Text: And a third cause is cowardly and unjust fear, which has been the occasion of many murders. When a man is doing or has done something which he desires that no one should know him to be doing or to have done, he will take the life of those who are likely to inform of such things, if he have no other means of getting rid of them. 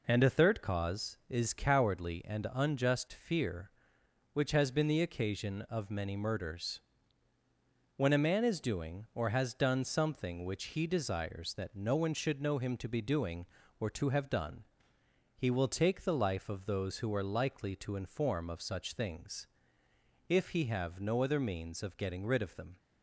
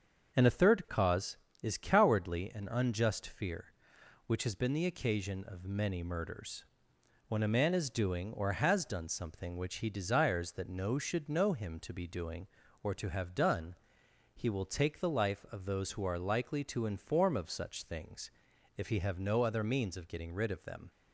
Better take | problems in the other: first | starts louder than the rest; until 1.6 s; 7 dB // skips "one"; at 10.9 s

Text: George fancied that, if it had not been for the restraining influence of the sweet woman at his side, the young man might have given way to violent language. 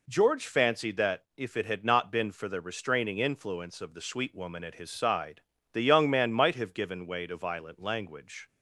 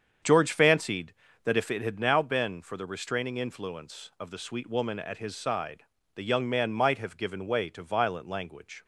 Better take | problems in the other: first | starts louder than the rest; strong; until 1.5 s; 7.5 dB // says "now" for "not"; at 1.9 s

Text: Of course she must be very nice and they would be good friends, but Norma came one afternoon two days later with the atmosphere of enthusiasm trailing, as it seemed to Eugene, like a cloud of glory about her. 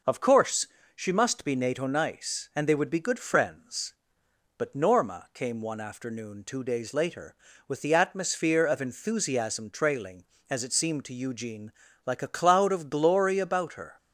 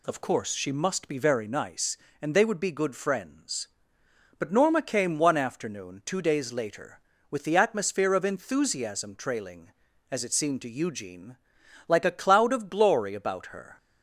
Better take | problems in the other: second | pauses between "course" and "she"; slight; at 0.6 s; 0.28 s long // says "nato" for "very"; at 1.5 s

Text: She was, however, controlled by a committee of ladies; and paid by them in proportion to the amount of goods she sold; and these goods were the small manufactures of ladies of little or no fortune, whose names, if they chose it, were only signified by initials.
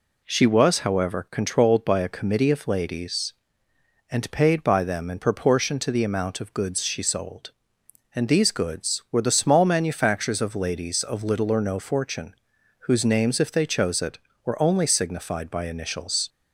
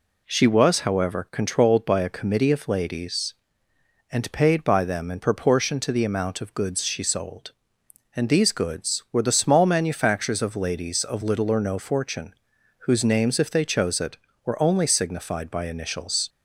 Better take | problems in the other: neither | none

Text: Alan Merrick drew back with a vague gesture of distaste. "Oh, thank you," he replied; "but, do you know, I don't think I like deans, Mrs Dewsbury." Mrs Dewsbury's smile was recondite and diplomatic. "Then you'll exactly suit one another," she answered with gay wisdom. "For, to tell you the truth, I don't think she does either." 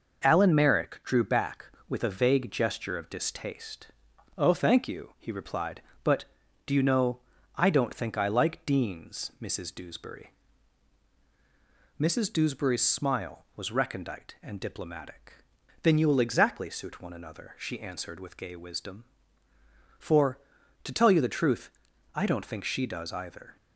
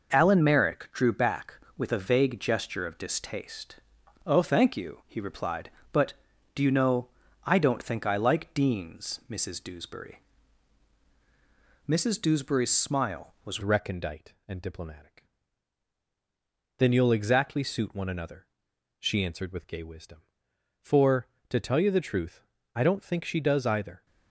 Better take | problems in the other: first | changes voice at "recondite"; from 13.6 s on; 10.4 s long

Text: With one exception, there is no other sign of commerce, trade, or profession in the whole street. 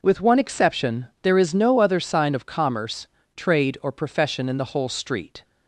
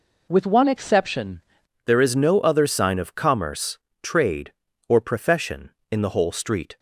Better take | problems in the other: first | changes voice at "there"; from 1.8 s on; 4.9 s long

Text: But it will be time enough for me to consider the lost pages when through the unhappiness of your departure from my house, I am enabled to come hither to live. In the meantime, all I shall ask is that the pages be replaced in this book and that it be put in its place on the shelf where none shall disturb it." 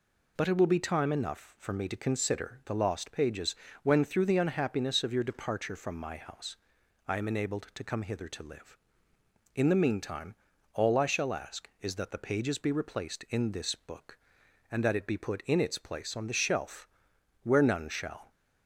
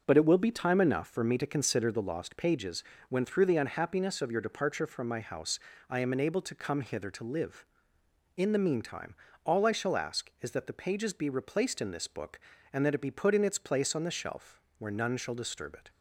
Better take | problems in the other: second | pauses between "pages" and "when"; slight; at 3.5 s; 0.28 s long; slight in the second // pauses between "shelf" and "where"; noticeable; at 16.8 s; 0.56 s long; slight in the second // stops before "disturb it"; at 18.3 s

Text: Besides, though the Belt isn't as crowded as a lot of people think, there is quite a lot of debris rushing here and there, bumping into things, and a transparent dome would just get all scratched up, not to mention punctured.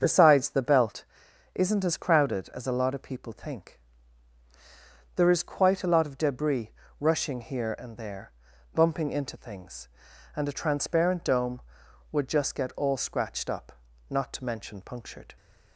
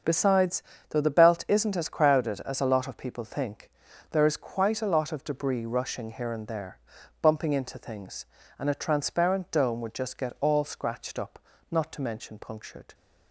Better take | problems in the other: second | starts louder than the rest; until 1.0 s; 7 dB; also in the second // skips "though"; at 0.4 s // pauses between "Belt" and "isn't"; noticeable; at 1.0 s; 0.50 s long // pauses between "debris" and "rushing"; slight; at 6.7 s; 0.26 s long

